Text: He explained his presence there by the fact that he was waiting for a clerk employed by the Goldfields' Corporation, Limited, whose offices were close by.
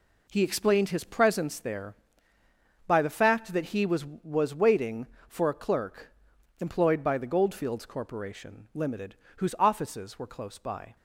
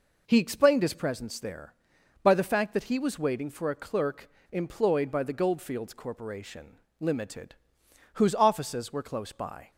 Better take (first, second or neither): second